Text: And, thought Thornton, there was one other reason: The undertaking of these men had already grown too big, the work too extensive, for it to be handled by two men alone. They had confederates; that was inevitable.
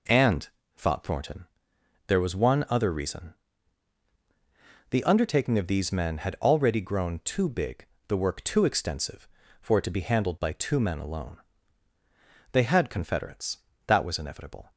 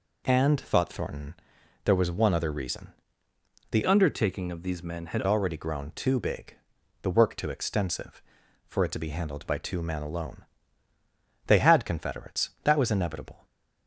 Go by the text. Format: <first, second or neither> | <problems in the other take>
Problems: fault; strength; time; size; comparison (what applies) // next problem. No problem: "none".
first | changes voice from "undertaking" to "had"; from 3.8 to 5.2 s; 1.4 s long